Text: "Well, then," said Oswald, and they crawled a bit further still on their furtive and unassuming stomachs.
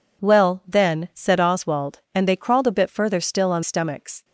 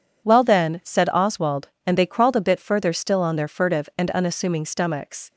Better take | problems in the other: second | skips "their furtive and unassuming"; at 3.6 s

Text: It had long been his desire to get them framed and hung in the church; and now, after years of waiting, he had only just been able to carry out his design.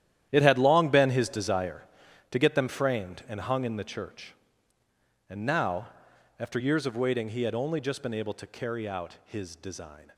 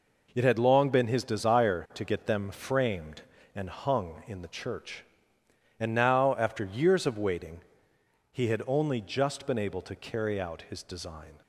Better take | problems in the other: second | gets quieter; strong; throughout; 13 dB

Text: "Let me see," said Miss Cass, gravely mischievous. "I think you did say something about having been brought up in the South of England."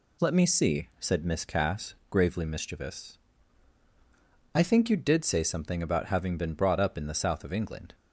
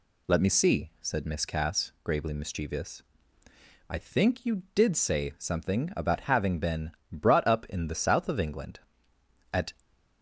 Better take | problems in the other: first | pauses between "been" and "brought"; slight; at 6.9 s; 0.20 s long // goes on to say "At"; slight; from 9.5 s on; 0.22 s long

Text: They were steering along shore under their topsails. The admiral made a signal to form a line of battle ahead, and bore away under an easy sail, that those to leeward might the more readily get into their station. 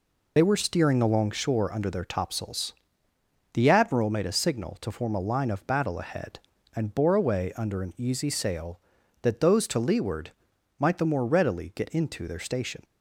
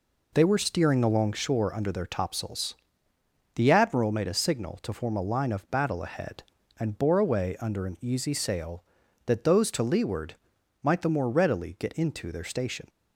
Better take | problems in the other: second | loses the start of "They"; at 0.3 s; 30 ms // pauses between "leeward" and "might"; noticeable; at 10.3 s; 0.48 s long; noticeable in the second

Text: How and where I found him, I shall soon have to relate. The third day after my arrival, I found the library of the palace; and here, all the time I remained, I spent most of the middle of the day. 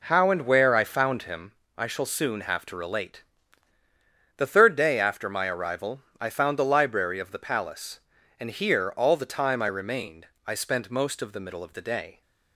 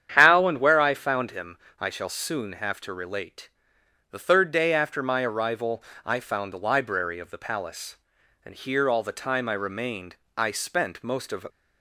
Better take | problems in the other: first | starts louder than the rest; strong; until 1.1 s; 9 dB // stops before "the middle of the day"; at 11.4 s

